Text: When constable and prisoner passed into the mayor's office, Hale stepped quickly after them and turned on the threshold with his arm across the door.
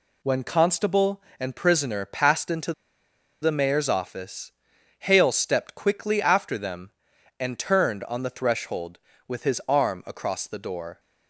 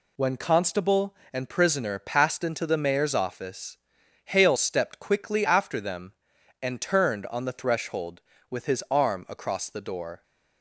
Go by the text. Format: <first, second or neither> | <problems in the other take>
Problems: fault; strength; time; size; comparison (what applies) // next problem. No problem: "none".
second | pauses between "into" and "the"; noticeable; at 2.7 s; 0.69 s long